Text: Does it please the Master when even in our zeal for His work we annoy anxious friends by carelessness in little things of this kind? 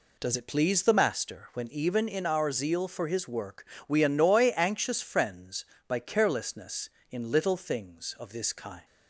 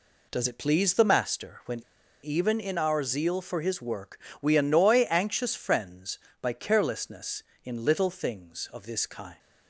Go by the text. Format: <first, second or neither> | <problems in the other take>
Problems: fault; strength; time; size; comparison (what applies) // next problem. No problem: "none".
first | pauses between "when" and "even"; at 1.8 s; 0.42 s long // pauses between "work" and "we"; slight; at 4.1 s; 0.24 s long; slight in the first